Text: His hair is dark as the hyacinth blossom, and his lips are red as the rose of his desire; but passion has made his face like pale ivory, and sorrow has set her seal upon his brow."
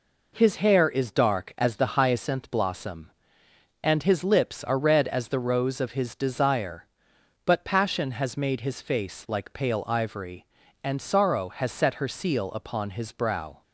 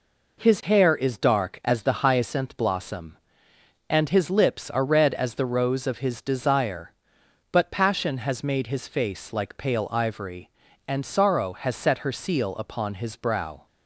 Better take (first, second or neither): neither